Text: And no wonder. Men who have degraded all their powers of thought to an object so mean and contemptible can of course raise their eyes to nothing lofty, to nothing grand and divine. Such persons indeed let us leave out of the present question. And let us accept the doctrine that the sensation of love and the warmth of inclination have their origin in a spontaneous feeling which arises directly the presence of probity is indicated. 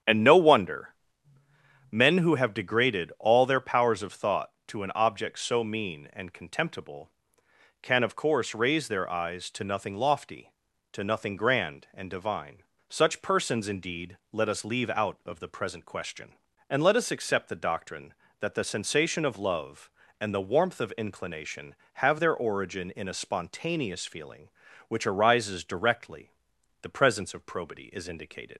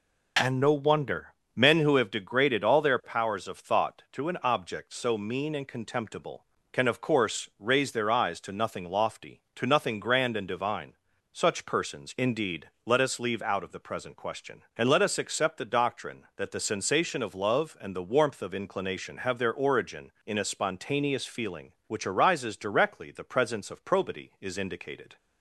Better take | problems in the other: second | starts louder than the rest; strong; until 2.0 s; 8.5 dB // pauses between "indeed" and "let"; slight; at 14.1 s; 0.16 s long; slight in the second // pauses between "directly" and "the"; noticeable; at 26.2 s; 0.52 s long // leaves "indicated" unfinished; at 28.5 s; 95 ms

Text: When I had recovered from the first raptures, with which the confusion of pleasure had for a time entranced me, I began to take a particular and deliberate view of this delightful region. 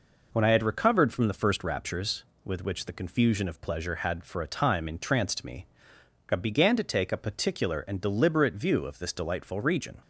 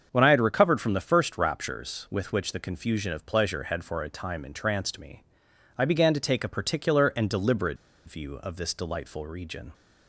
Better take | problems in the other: first | starts louder than the rest; until 1.1 s; 7 dB // pauses between "deliberate" and "view"; slight; at 7.7 s; 0.31 s long

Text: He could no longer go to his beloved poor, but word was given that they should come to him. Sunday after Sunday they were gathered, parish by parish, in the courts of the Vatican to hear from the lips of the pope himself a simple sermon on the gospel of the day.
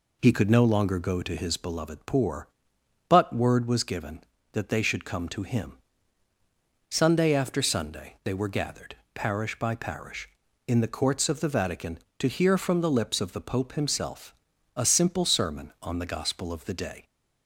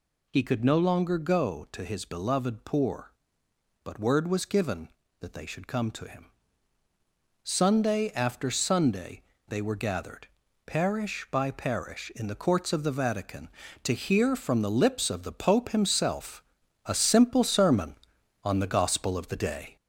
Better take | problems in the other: first | gets louder; noticeable; throughout; 4 dB // pauses between "Sunday" and "they"; slight; at 9.2 s; 0.26 s long // pauses between "himself" and "a"; at 16.4 s; 0.42 s long; also in the first

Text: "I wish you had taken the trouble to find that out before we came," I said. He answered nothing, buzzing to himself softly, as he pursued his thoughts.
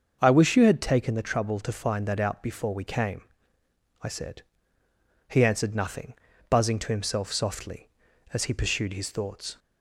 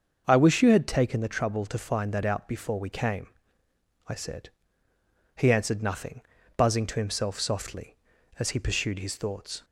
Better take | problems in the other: neither | starts louder than the rest; the same in both

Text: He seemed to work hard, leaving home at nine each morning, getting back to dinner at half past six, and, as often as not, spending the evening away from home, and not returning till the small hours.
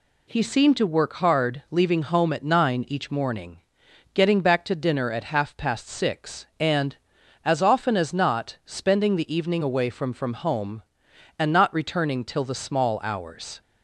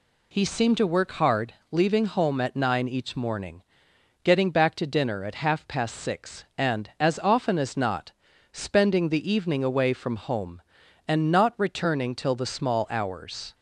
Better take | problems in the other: second | says "from" twice; at 10.1 s

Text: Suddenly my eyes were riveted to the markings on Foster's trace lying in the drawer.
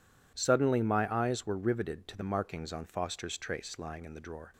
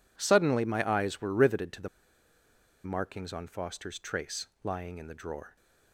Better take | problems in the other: first | pauses between "the" and "markings"; noticeable; at 1.8 s; 0.97 s long // pauses between "trace" and "lying"; slight; at 4.4 s; 0.16 s long

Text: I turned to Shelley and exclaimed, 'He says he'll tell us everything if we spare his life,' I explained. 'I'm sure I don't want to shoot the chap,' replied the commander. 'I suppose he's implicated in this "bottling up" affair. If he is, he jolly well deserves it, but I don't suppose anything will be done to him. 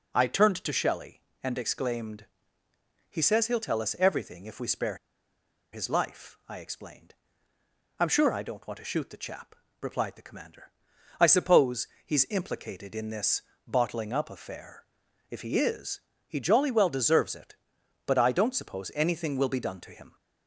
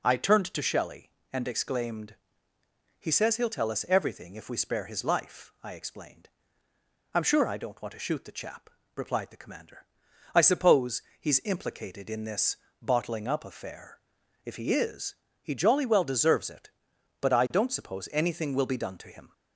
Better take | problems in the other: second | pauses between "spare" and "his"; noticeable; at 4.9 s; 0.76 s long // pauses between "suppose" and "he's"; slight; at 11.8 s; 0.18 s long; slight in the second // pauses between "this" and "bottling"; slight; at 13.4 s; 0.26 s long; slight in the second

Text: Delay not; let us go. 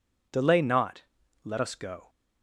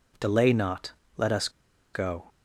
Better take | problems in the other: first | pauses between "us" and "go"; at 1.4 s; 0.44 s long

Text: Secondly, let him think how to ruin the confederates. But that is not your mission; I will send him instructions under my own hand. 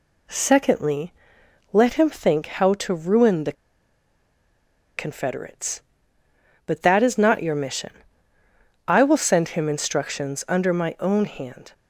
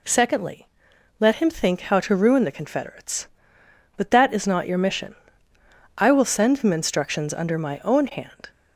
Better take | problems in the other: second | pauses between "the" and "confederates"; strong; at 3.5 s; 1.4 s long

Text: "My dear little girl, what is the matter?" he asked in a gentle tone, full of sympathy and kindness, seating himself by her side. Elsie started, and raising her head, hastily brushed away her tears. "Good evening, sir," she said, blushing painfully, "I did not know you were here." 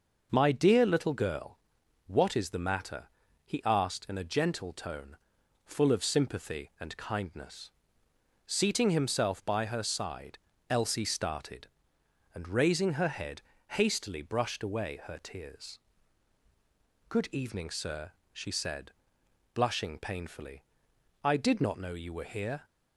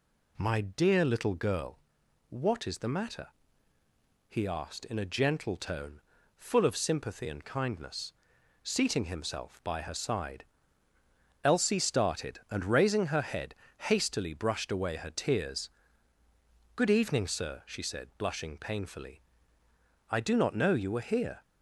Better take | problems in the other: first | says "do" for "did"; at 20.1 s

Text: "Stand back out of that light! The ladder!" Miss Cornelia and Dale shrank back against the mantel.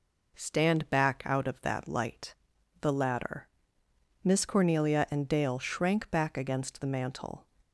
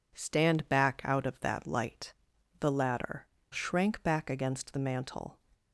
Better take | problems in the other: first | skips "Miss Cornelia and Dale"; at 3.3 s

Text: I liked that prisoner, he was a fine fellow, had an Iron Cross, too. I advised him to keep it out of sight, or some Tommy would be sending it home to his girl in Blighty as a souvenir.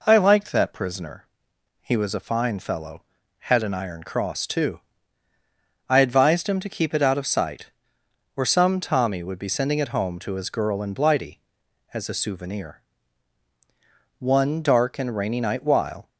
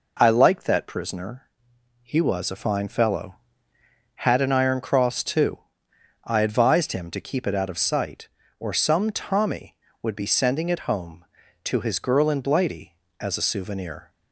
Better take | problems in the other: second | goes on to say "One dark and rainy night while"; strong; from 14.1 s on; 1.9 s long

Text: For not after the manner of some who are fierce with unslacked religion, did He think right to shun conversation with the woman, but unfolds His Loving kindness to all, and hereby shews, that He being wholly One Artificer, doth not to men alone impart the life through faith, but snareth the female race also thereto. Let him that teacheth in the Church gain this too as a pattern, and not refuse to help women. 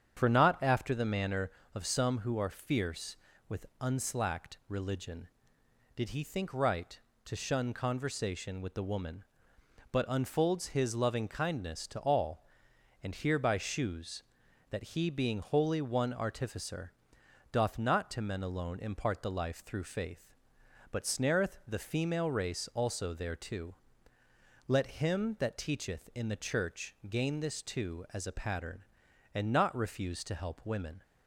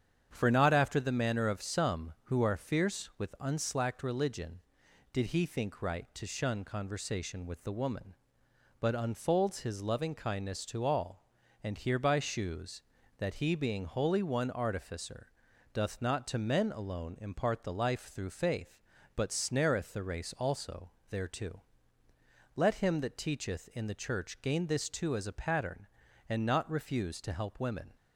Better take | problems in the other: first | starts louder than the rest; strong; until 1.3 s; 8.5 dB; strong in the first // skips "female"; at 20.0 s // pauses between "also" and "thereto"; slight; at 20.9 s; 0.18 s long

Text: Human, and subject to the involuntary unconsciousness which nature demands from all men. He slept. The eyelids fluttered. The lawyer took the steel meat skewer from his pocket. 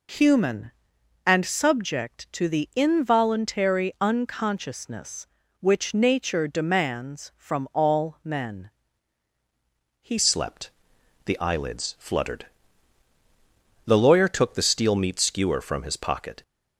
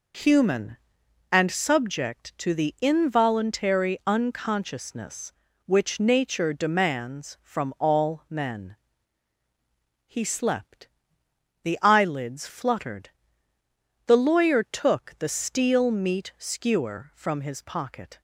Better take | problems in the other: second | changes voice at "slept"; from 10.1 s on; 6.3 s long

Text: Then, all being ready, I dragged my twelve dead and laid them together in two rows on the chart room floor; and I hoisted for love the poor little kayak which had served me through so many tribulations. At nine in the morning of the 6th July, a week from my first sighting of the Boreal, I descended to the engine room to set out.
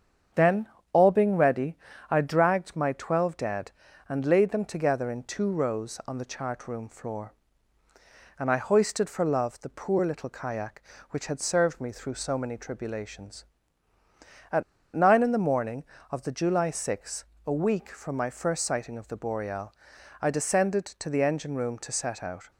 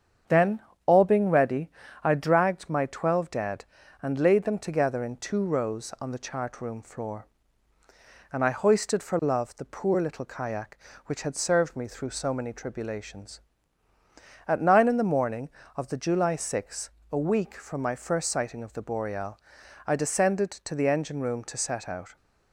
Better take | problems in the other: second | starts louder than the rest; strong; until 1.5 s; 7.5 dB; strong in the second // pauses between "At" and "nine"; slight; at 14.6 s; 0.30 s long

